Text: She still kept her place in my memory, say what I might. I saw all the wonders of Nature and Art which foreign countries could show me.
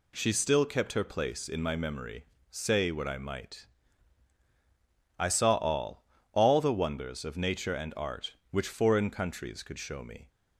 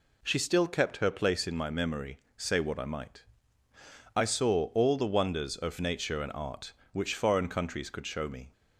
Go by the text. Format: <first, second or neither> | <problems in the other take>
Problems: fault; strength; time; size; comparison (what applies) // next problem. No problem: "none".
second | says "all" twice; at 6.3 s